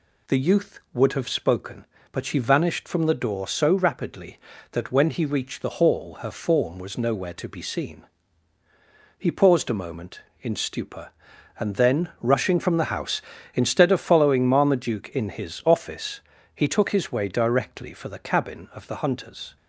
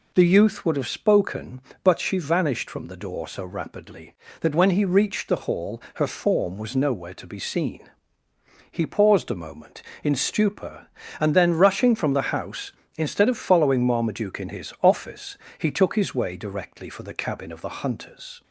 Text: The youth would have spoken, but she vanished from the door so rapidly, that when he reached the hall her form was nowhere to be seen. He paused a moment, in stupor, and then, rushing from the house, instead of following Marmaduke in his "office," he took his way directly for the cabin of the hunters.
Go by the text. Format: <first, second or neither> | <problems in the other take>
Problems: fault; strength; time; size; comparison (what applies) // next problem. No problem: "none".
neither | none